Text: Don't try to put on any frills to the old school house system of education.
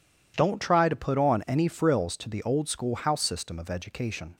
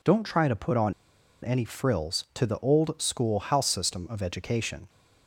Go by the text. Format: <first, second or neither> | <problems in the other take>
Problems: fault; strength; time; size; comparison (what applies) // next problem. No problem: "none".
first | pauses between "on" and "any"; noticeable; at 0.9 s; 0.51 s long